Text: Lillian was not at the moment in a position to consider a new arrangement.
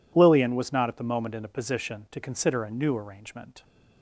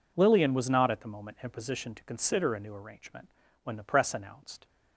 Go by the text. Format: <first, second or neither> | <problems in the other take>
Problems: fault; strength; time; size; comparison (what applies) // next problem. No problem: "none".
first | goes on to say "When the press announced"; noticeable; from 3.6 s on; 1.0 s long